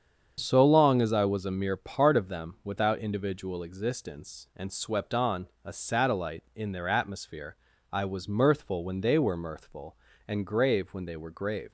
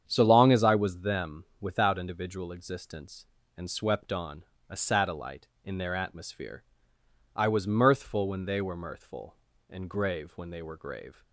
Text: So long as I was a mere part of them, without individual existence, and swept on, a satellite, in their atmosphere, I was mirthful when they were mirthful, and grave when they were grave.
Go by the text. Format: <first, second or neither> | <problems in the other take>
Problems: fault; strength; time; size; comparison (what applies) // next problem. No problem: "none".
first | starts louder than the rest; strong; until 1.0 s; 8.5 dB; strong in the first // skips "a mere part of"; at 1.0 s